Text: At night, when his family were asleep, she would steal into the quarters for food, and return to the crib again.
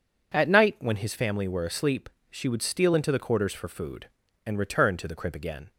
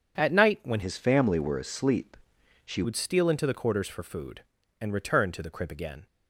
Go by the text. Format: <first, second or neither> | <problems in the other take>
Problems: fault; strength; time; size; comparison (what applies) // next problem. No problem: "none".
first | changes voice from "his" to "she"; from 0.8 to 2.8 s; 2.0 s long